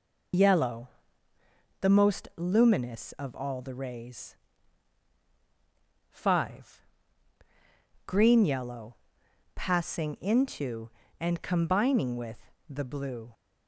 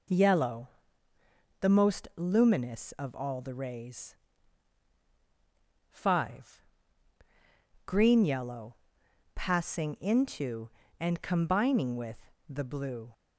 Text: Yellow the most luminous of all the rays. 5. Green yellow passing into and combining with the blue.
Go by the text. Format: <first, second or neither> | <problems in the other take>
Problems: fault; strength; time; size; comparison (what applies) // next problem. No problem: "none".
second | loses the start of "Yellow"; at 0.3 s; 55 ms // pauses between "Yellow" and "the"; noticeable; at 0.8 s; 0.92 s long; noticeable in the second // pauses between "yellow" and "passing"; noticeable; at 8.9 s; 0.60 s long; noticeable in the second // pauses between "with" and "the"; slight; at 12.5 s; 0.18 s long; slight in the second